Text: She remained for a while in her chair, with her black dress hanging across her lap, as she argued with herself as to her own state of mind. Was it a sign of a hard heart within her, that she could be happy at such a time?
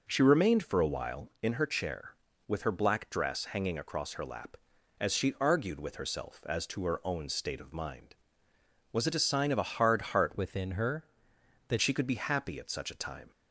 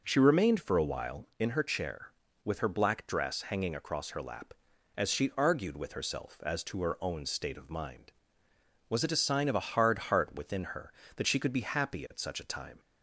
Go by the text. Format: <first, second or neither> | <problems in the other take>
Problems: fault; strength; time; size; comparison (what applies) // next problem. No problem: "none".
second | changes voice from "within" to "that"; from 10.3 to 11.7 s; 1.4 s long